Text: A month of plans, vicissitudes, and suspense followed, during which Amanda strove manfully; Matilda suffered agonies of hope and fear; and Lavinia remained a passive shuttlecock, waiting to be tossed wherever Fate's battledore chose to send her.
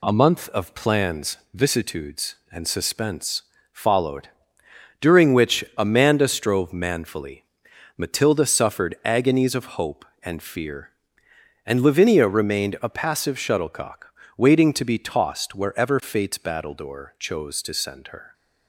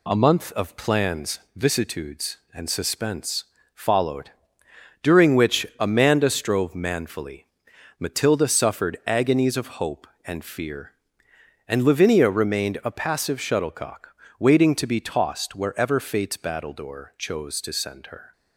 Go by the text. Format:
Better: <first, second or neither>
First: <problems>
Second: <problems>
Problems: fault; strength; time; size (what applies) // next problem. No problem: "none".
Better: neither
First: pauses between "suspense" and "followed"; slight; at 3.4 s; 0.28 s long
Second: pauses between "suspense" and "followed"; slight; at 3.4 s; 0.28 s long